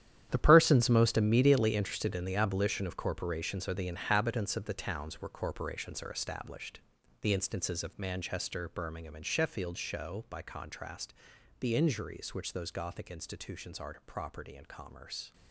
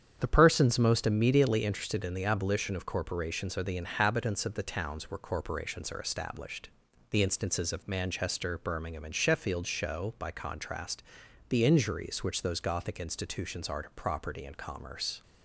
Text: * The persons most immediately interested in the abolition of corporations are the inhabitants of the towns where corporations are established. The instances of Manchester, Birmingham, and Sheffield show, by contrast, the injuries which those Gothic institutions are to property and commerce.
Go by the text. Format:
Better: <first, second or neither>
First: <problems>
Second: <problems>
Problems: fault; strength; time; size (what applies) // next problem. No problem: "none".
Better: second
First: gets quieter; strong; throughout; 13 dB // starts louder than the rest; strong; until 1.3 s; 10.5 dB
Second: starts louder than the rest; strong; until 1.2 s; 8.5 dB